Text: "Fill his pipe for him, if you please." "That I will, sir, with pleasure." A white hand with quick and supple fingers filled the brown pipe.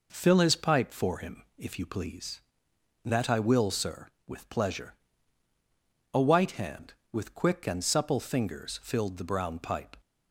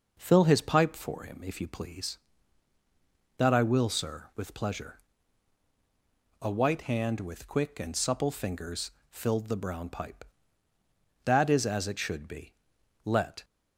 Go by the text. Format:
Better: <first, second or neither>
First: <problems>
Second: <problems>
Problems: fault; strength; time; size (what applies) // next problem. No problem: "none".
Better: first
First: none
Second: pauses between "fingers" and "filled"; slight; at 8.8 s; 0.18 s long // goes on to say "That is as it should be Let"; strong; from 11.2 s on; 2.2 s long